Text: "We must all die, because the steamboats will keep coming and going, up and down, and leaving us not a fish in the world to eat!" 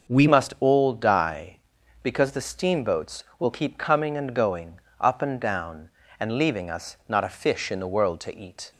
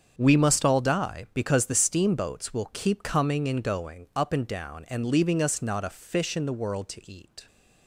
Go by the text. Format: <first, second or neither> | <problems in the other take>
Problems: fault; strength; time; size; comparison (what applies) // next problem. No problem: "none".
second | starts louder than the rest; noticeable; until 1.1 s; 6 dB; strong in the second // changes voice at "must"; from 0.2 s on; 8.5 s long